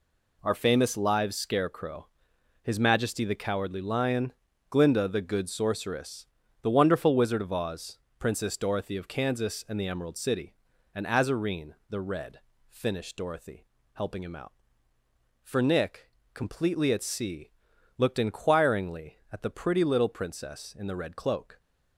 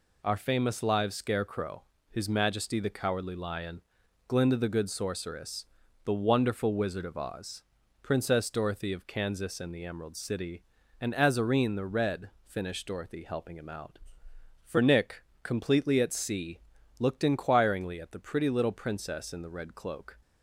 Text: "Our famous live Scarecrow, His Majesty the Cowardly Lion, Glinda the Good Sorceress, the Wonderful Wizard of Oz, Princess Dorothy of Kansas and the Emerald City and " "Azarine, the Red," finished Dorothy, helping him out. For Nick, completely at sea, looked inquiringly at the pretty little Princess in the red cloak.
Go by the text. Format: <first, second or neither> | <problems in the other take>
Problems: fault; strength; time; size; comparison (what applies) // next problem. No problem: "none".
neither | none